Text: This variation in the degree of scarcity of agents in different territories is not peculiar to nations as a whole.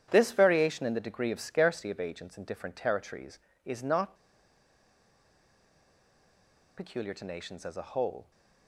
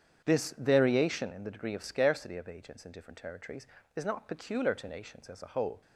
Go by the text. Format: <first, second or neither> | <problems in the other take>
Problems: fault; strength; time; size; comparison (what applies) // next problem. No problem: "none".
second | starts louder than the rest; strong; until 1.1 s; 10 dB; strong in the second // pauses between "not" and "peculiar"; strong; at 4.1 s; 2.6 s long